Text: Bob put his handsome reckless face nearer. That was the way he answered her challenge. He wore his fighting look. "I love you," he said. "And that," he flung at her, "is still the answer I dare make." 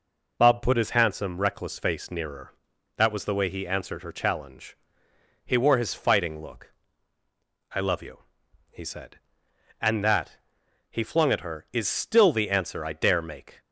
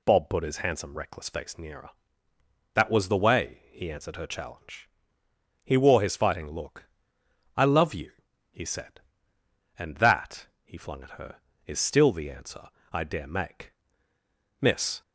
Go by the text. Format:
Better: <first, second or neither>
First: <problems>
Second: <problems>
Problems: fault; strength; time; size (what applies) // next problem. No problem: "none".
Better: first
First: none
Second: pauses between "answer" and "I"; slight; at 12.6 s; 0.22 s long // goes on to say "Miss"; slight; from 14.6 s on; 0.40 s long